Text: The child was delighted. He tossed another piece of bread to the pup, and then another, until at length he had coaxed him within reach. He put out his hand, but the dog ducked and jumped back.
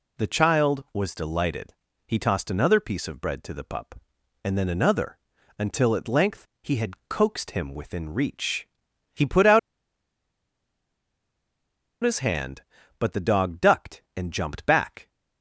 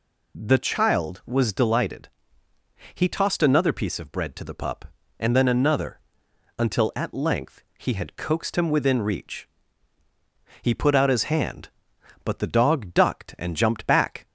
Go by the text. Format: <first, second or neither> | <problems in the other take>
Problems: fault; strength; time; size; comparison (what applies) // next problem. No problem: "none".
second | pauses between "out" and "his"; strong; at 9.5 s; 2.4 s long